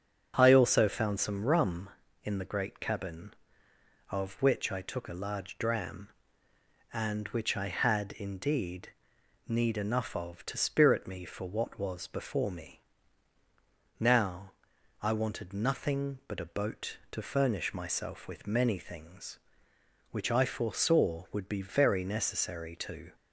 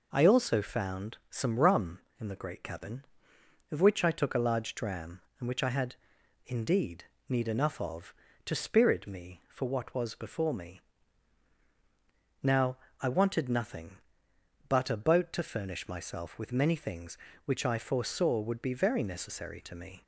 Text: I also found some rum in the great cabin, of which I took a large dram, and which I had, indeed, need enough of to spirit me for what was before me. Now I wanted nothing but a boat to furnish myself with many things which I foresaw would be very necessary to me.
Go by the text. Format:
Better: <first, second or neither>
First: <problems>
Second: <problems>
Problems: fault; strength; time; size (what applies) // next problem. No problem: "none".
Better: second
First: starts louder than the rest; until 1.3 s; 7 dB // pauses between "Now" and "I"; noticeable; at 14.5 s; 0.50 s long // stops before "me"; at 23.1 s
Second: pauses between "Now" and "I"; slight; at 12.7 s; 0.24 s long